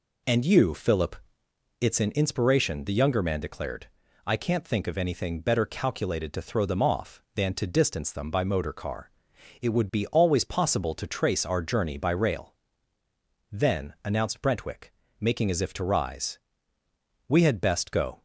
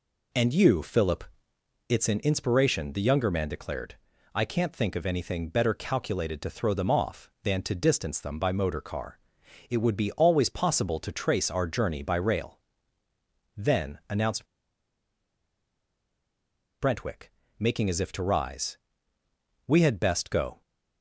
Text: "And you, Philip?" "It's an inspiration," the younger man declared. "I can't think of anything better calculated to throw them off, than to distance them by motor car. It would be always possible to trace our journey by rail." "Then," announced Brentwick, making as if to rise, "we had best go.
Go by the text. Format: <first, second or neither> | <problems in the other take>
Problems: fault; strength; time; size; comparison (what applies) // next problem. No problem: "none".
first | pauses between "announced" and "Brentwick"; strong; at 14.4 s; 2.3 s long